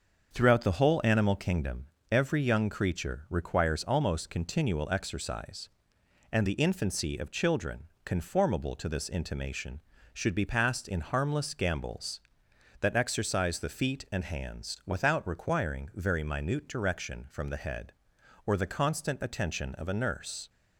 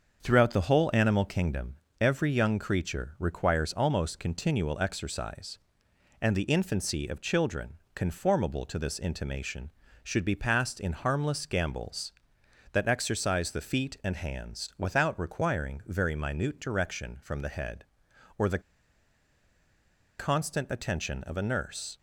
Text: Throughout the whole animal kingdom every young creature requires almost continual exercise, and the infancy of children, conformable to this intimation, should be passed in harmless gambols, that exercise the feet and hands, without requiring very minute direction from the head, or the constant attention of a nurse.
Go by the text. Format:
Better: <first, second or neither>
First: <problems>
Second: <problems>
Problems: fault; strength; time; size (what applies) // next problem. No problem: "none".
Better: first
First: starts louder than the rest; until 1.3 s; 6.5 dB // pauses between "kingdom" and "every"; slight; at 1.8 s; 0.22 s long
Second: starts louder than the rest; until 1.2 s; 6.5 dB // pauses between "kingdom" and "every"; slight; at 1.7 s; 0.22 s long // pauses between "the" and "constant"; strong; at 18.6 s; 1.5 s long